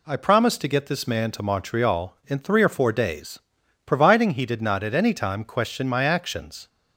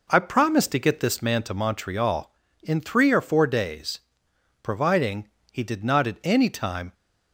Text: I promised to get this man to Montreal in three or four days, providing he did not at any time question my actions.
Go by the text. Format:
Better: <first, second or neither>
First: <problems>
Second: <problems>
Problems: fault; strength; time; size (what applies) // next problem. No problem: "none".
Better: first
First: none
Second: pauses between "providing" and "he"; slight; at 5.2 s; 0.24 s long // stops before "question my actions"; at 6.9 s